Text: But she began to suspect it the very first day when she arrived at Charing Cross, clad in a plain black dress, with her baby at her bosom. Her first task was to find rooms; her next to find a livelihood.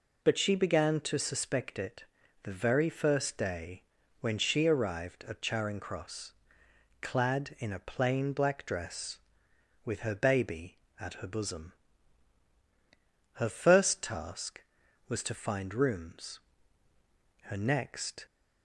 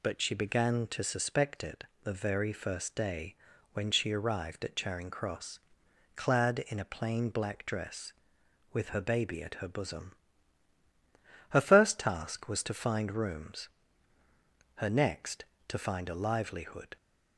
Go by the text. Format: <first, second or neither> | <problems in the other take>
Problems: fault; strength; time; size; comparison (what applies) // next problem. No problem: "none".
second | pauses between "it" and "the"; at 2.0 s; 0.40 s long; slight in the second // pauses between "day" and "when"; at 3.8 s; 0.38 s long; also in the second // stops before "to find a livelihood"; at 18.2 s